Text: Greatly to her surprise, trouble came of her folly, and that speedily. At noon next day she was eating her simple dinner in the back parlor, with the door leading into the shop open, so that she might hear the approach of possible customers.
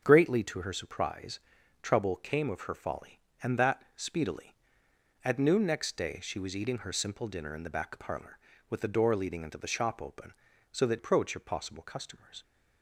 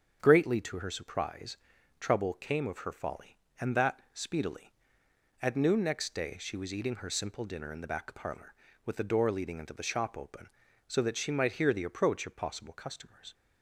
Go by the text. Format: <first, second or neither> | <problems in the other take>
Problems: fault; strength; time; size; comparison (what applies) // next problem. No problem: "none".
second | starts louder than the rest; until 1.0 s; 7 dB; also in the second // skips "she might hear the"; at 10.9 s